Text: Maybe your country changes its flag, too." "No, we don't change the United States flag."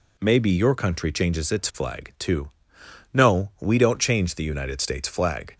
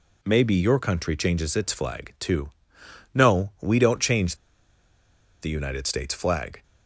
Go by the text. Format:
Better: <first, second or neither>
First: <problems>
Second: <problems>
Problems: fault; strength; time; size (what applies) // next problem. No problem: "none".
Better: first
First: none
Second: pauses between "change" and "the"; at 4.3 s; 1.0 s long